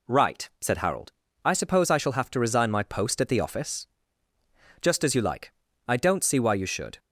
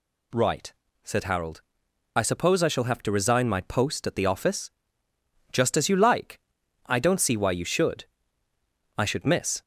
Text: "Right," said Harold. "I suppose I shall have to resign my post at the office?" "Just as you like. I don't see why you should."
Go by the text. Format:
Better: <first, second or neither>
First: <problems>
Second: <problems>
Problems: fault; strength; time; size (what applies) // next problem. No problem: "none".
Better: first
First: none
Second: goes on to say "I should miss"; noticeable; from 8.9 s on; 0.64 s long